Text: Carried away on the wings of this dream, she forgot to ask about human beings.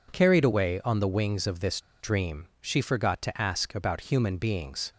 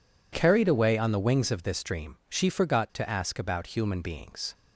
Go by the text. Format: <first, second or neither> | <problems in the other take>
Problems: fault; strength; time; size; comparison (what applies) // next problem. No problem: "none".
second | pauses between "this" and "dream"; slight; at 1.7 s; 0.20 s long